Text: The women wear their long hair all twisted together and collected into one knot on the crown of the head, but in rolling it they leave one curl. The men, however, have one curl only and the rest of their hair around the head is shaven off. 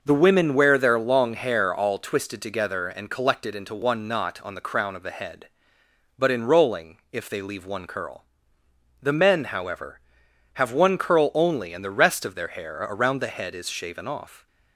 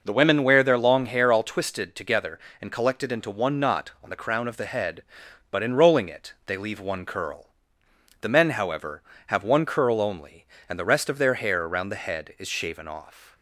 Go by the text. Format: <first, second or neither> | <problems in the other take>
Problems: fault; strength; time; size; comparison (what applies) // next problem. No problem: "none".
second | says "if" for "it"; at 7.1 s